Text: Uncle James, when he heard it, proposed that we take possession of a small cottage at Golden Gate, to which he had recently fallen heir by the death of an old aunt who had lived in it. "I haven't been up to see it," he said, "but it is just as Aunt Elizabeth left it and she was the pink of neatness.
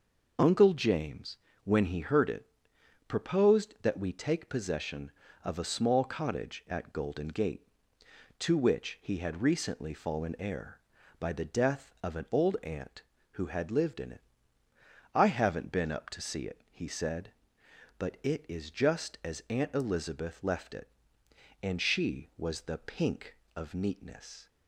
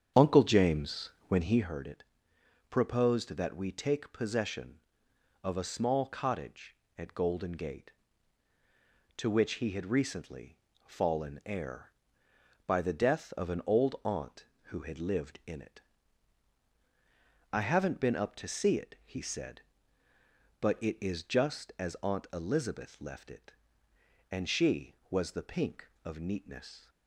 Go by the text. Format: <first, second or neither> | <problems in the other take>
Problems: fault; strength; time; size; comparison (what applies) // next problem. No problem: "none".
first | starts louder than the rest; strong; until 1.8 s; 8.5 dB // pauses between "recently" and "fallen"; slight; at 10.5 s; 0.30 s long